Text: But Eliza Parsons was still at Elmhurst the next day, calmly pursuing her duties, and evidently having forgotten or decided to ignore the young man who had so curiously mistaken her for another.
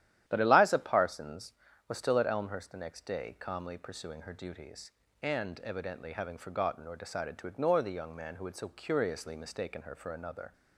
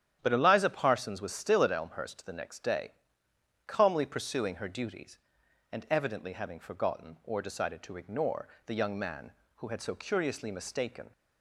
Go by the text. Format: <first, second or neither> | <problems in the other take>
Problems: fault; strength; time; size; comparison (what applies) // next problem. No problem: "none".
first | starts louder than the rest; strong; until 1.2 s; 10 dB; strong in the first // pauses between "ignore" and "the"; slight; at 8.4 s; 0.16 s long // stops before "her for another"; at 11.1 s